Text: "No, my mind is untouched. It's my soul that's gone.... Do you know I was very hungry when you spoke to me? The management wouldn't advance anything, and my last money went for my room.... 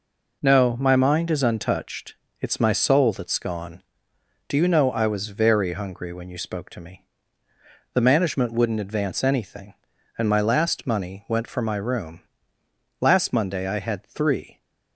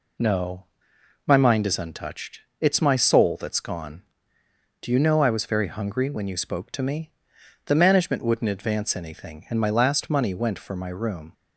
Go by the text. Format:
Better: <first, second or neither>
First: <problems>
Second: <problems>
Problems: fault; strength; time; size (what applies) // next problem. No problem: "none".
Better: second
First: goes on to say "Last Monday I had three"; from 13.0 s on; 1.5 s long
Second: none